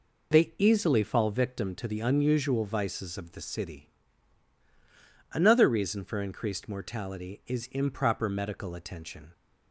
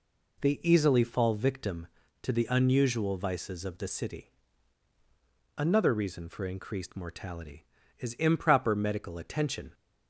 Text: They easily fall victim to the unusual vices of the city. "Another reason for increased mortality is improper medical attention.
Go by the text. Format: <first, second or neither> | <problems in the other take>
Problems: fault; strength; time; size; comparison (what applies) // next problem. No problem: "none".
neither | none